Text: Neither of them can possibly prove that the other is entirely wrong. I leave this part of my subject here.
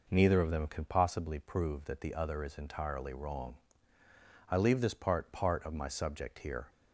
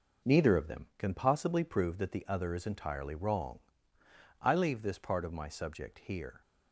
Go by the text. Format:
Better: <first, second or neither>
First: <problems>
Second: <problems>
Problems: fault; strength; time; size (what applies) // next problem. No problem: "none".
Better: second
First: says "part" twice; at 5.3 s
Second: none